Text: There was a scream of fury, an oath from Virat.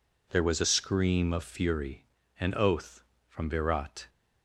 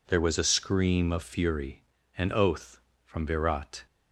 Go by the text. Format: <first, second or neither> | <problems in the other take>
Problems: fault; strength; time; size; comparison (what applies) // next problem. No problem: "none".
neither | none